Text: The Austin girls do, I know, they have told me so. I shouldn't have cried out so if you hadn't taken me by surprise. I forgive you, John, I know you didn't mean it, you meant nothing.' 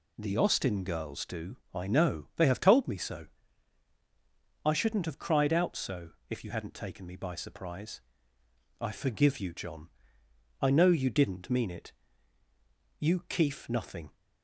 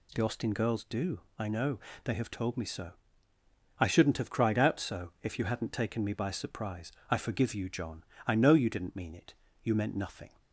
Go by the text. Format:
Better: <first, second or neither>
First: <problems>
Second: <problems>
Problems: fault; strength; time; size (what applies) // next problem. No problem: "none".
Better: second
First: pauses between "so" and "if"; slight; at 6.0 s; 0.20 s long // says "keef" for "meant"; at 13.2 s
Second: none